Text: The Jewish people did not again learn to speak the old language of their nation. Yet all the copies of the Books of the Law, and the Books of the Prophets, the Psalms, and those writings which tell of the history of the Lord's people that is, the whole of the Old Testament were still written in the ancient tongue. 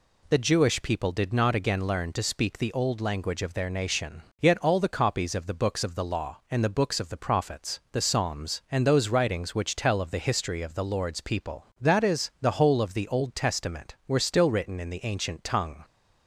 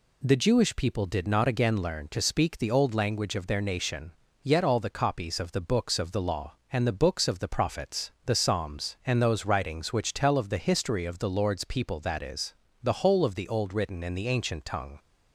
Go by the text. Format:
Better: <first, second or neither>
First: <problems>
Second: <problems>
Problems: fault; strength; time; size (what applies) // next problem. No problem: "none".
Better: first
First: none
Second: skips "Testament were still"; at 13.7 s